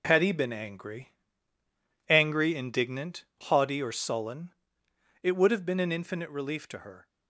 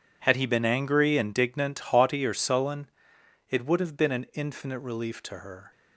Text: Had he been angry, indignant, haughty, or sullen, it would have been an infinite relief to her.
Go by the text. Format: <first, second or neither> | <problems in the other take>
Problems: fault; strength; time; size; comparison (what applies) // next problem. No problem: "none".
second | says "angry" twice; at 2.0 s